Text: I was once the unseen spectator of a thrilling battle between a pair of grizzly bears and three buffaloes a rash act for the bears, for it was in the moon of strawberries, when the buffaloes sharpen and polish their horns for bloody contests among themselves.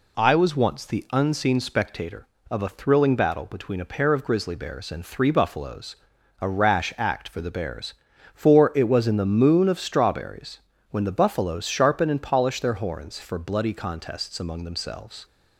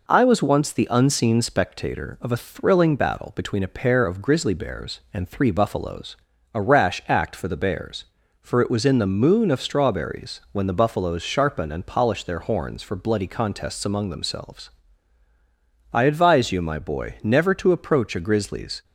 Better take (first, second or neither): first